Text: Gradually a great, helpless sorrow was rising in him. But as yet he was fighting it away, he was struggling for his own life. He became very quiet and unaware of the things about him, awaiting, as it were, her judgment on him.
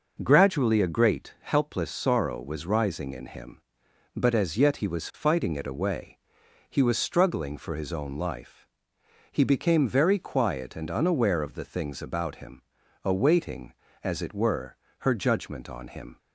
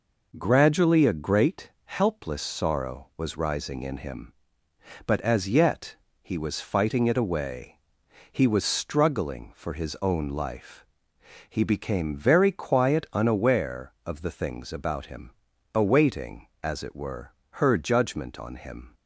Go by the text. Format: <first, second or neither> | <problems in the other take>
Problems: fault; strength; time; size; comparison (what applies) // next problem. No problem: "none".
first | pauses between "yet" and "he"; slight; at 5.9 s; 0.26 s long // skips "and"; at 13.0 s